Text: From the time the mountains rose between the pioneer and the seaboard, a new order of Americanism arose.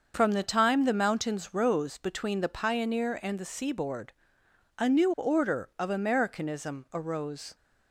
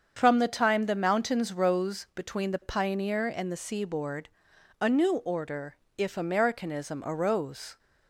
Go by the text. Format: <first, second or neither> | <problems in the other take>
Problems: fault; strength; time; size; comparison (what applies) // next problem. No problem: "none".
first | starts louder than the rest; until 1.2 s; 7 dB; also in the first // says "if" for "of"; at 5.9 s